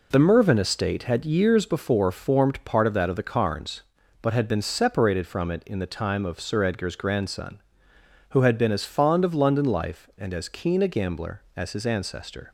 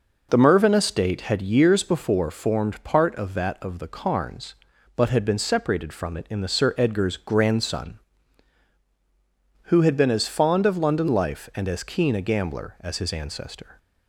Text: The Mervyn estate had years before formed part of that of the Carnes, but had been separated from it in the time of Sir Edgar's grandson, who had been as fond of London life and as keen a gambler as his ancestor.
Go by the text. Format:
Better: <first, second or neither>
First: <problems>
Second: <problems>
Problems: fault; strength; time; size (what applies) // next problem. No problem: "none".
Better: first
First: none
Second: skips "time of"; at 6.4 s